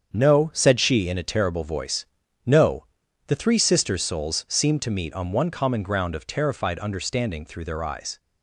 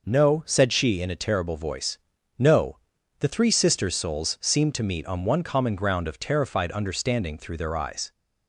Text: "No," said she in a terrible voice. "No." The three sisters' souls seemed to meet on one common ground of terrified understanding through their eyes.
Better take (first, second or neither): second